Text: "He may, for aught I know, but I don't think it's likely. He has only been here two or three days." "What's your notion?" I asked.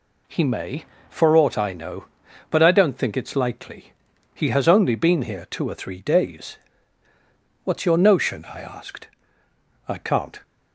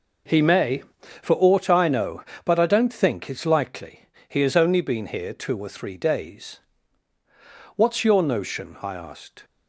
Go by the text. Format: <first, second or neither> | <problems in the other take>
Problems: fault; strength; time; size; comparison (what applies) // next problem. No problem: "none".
second | goes on to say "I can't"; from 9.8 s on; 0.54 s long